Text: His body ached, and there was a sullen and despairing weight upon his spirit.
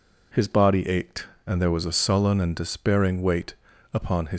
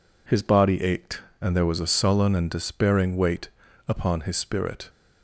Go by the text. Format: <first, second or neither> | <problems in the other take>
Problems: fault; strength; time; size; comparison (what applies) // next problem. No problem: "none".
second | pauses between "weight" and "upon"; at 3.5 s; 0.40 s long; also in the second // stops before "spirit"; at 4.3 s